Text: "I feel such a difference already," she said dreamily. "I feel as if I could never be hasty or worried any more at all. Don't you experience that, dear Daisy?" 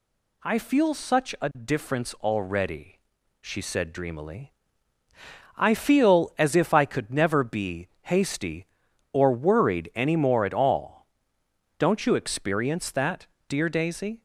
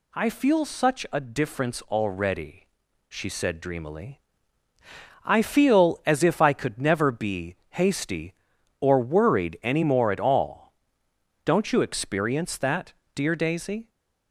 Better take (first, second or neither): neither